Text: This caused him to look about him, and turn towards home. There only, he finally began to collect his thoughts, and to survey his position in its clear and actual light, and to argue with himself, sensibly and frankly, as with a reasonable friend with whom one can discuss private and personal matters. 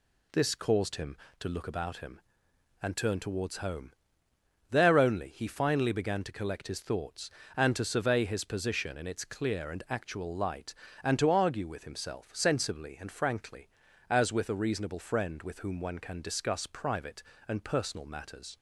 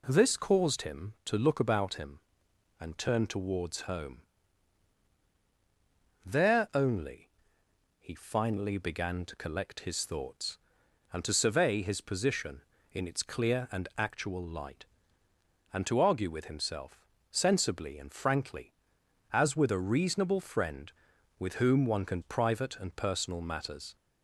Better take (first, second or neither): first